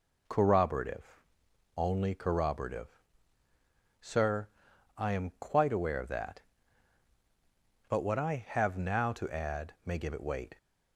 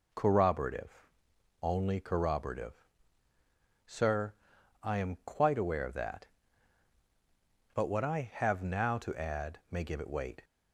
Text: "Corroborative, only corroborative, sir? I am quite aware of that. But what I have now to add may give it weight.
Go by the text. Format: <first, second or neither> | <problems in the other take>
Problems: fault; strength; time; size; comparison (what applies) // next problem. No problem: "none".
neither | none